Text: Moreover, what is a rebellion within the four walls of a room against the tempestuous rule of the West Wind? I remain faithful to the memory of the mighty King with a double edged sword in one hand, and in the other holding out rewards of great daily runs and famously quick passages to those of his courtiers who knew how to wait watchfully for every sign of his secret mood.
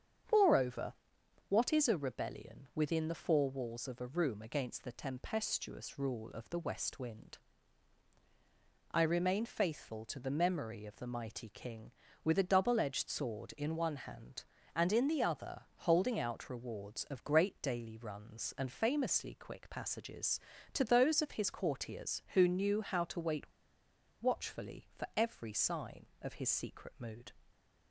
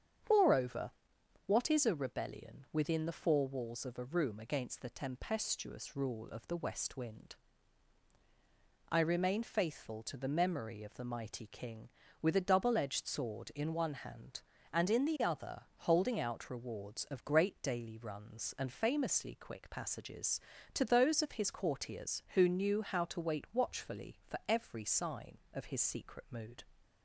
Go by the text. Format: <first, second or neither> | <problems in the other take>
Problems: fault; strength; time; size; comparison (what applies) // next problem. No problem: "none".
second | starts louder than the rest; strong; until 1.8 s; 7.5 dB; strong in the second // pauses between "other" and "holding"; slight; at 15.6 s; 0.16 s long; slight in the second // pauses between "wait" and "watchfully"; noticeable; at 23.4 s; 0.74 s long